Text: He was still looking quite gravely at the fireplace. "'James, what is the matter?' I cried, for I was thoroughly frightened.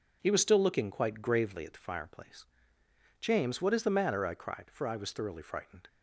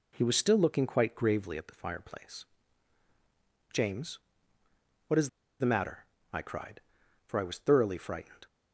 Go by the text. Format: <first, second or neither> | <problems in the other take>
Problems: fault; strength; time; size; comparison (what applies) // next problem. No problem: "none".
first | pauses between "is" and "the"; slight; at 5.2 s; 0.32 s long